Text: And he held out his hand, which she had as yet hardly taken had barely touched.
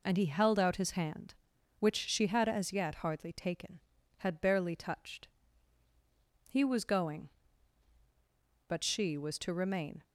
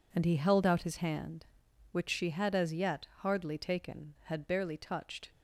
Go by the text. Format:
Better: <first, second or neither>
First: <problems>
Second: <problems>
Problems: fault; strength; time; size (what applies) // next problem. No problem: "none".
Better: second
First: goes on to say "He was going but she was to remain"; strong; from 6.5 s on; 3.5 s long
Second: none